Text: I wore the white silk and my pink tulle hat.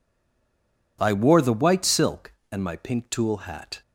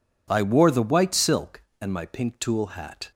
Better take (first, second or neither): second